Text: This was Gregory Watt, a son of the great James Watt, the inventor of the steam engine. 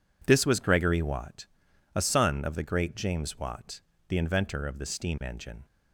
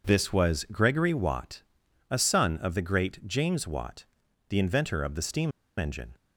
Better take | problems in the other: first | pauses between "steam" and "engine"; slight; at 5.5 s; 0.26 s long

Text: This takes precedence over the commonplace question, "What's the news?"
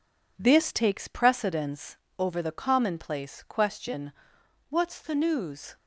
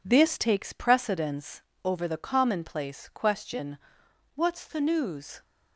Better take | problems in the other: neither | pauses between "precedence" and "over"; slight; the same in both

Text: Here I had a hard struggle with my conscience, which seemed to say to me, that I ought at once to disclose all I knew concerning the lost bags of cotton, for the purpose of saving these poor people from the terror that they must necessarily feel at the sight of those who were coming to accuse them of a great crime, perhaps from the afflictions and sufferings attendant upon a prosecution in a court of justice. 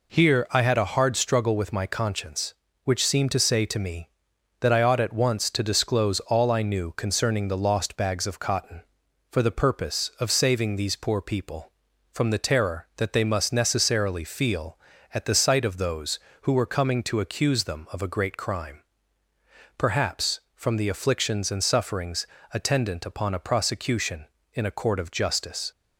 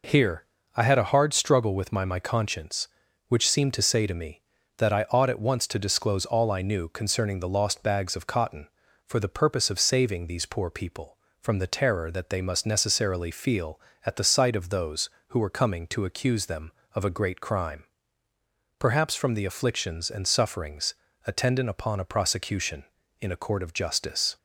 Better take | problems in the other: first | pauses between "Here" and "I"; slight; at 0.4 s; 0.32 s long // says "my" twice; at 2.0 s // pauses between "sufferings" and "attendant"; slight; at 20.9 s; 0.32 s long; slight in the first

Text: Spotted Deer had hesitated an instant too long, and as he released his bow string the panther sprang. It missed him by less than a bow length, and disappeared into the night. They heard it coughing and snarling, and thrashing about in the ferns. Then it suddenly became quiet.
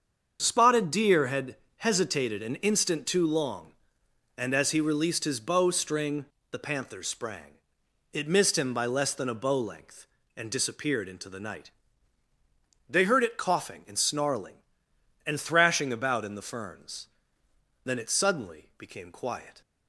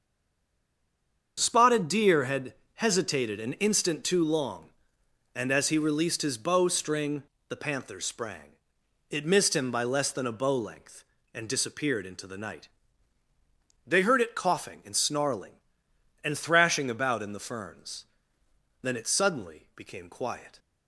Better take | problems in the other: first | stays silent before the first word; noticeable; until 1.3 s; 1.3 s long // starts louder than the rest; until 2.4 s; 7 dB; also in the first // pauses between "had" and "hesitated"; slight; at 2.5 s; 0.22 s long; slight in the first // pauses between "string" and "the"; slight; at 7.2 s; 0.24 s long; slight in the first

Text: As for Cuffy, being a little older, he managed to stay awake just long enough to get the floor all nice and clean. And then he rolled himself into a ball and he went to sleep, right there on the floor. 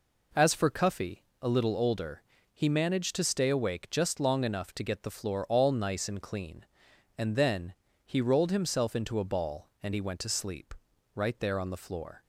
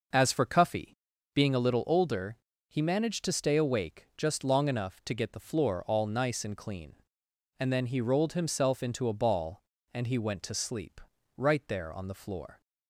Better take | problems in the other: second | skips "being"; at 1.3 s // pauses between "then" and "he"; slight; at 7.7 s; 0.32 s long

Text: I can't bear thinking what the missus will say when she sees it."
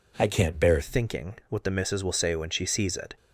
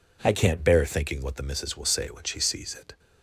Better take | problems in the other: second | changes voice at "thinking"; from 0.8 s on; 2.3 s long

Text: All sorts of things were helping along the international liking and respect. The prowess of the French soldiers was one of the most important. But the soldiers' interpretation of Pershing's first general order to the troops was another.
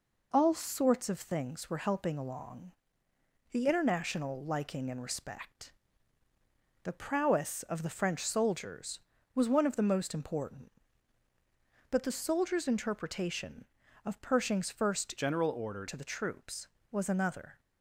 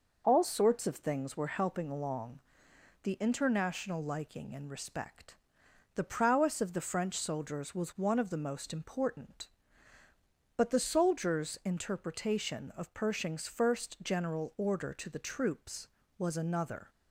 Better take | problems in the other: second | pauses between "along" and "the"; noticeable; at 2.7 s; 0.80 s long; noticeable in the second // changes voice from "general" to "order"; from 15.1 to 15.8 s; 0.7 s long

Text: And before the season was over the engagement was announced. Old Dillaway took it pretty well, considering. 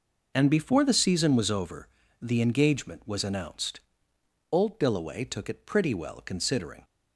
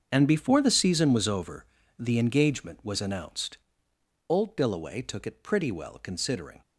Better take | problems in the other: first | gets quieter; strong; throughout; 13 dB // pauses between "over" and "the"; slight; at 1.6 s; 0.34 s long; slight in the first

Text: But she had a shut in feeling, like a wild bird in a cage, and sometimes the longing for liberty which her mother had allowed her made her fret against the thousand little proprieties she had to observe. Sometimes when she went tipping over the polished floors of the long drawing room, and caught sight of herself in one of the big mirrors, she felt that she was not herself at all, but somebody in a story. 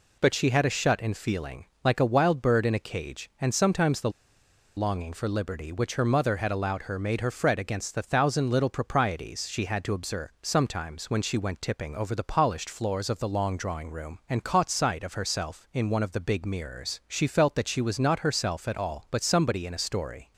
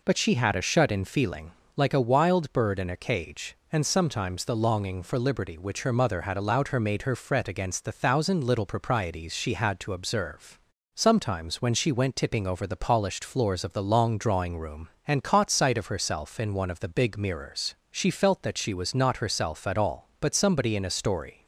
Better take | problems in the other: second | pauses between "the" and "longing"; noticeable; at 4.0 s; 0.66 s long

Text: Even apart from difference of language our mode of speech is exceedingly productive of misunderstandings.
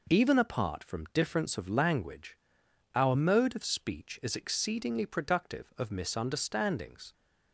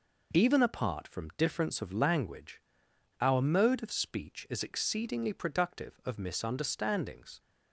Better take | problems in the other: neither | pauses between "language" and "our"; noticeable; the same in both

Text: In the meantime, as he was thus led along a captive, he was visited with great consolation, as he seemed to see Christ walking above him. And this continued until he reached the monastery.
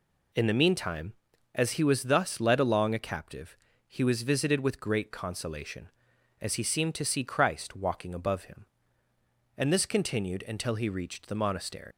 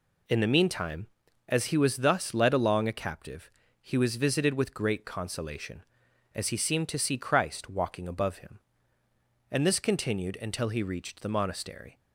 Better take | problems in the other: second | leaves "monastery" unfinished; at 11.9 s; 130 ms

